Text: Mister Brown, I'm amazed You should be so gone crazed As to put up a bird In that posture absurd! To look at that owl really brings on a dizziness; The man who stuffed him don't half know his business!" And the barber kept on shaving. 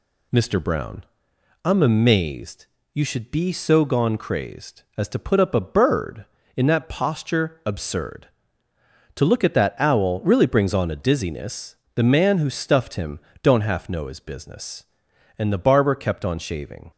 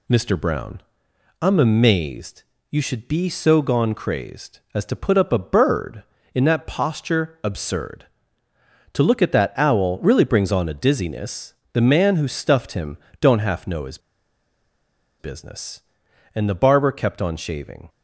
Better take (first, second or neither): first